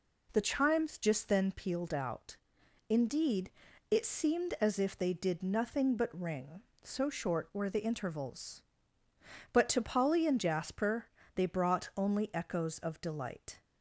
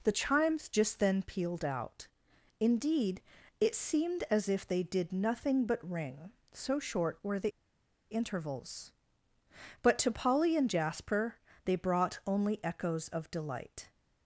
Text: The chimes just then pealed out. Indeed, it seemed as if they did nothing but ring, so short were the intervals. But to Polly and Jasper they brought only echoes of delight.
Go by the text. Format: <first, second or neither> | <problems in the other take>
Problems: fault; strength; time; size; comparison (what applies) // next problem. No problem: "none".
first | pauses between "the" and "intervals"; noticeable; at 7.5 s; 0.62 s long // pauses between "Jasper" and "they"; slight; at 11.3 s; 0.30 s long; slight in the first